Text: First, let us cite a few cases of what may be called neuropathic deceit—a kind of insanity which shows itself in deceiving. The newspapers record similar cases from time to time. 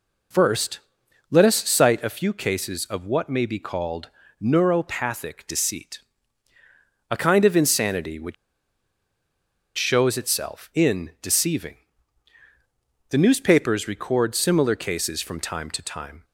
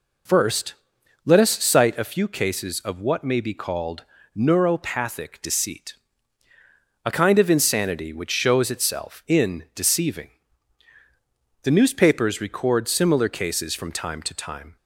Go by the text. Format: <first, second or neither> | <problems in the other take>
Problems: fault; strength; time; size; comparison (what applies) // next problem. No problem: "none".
second | pauses between "called" and "neuropathic"; slight; at 4.0 s; 0.34 s long; slight in the second // pauses between "which" and "shows"; strong; at 8.3 s; 1.4 s long